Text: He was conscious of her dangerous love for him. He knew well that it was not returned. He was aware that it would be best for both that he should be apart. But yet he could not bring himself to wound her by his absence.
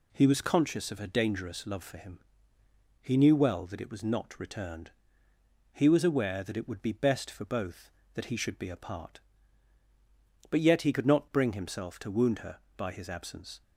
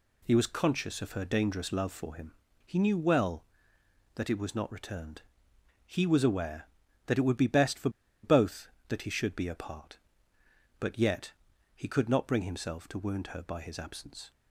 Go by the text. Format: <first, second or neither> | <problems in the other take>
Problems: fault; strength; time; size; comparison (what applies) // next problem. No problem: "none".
first | pauses between "for" and "both"; slight; at 7.8 s; 0.33 s long // pauses between "yet" and "he"; at 11.3 s; 0.42 s long